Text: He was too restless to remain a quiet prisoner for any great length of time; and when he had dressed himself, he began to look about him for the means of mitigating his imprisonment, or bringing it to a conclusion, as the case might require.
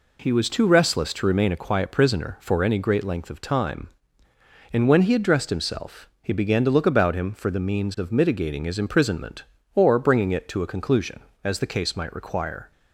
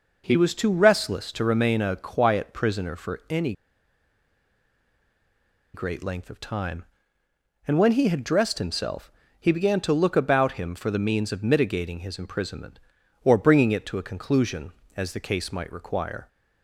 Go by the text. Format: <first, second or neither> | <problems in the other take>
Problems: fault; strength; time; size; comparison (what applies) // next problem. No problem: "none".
first | pauses between "any" and "great"; strong; at 3.5 s; 2.2 s long